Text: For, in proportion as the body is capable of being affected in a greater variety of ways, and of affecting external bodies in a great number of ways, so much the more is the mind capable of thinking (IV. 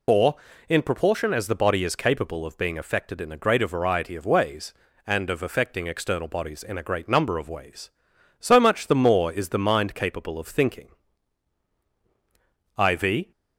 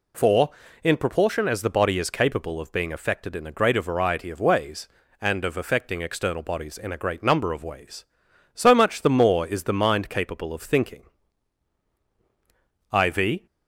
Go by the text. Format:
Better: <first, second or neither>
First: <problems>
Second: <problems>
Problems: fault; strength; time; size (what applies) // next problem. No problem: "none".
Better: second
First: loses the start of "For"; at 0.0 s; 80 ms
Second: none